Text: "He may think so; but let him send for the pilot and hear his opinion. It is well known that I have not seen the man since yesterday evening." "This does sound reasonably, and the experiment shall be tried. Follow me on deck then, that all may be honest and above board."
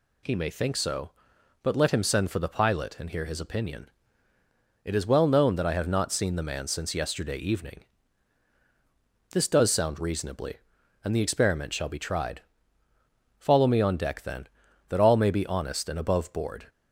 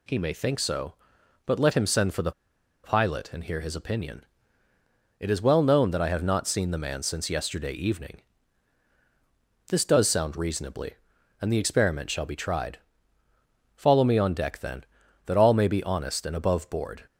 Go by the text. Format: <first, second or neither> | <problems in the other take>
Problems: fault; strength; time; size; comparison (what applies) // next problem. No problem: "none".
first | pauses between "the" and "pilot"; noticeable; at 2.3 s; 0.52 s long